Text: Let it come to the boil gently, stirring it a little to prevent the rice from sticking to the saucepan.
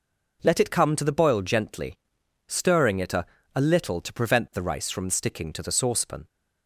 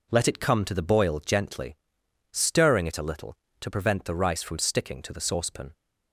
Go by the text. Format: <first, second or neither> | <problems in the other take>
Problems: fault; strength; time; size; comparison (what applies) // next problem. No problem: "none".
second | says "a" twice; at 3.5 s